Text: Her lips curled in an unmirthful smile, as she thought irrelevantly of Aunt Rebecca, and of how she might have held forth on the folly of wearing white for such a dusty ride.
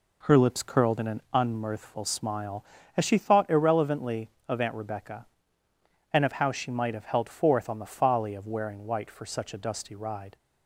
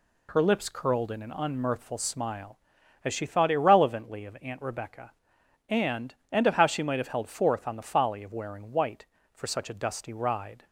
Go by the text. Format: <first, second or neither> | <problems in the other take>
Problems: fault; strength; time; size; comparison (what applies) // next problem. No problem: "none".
first | says "and" twice; at 6.2 s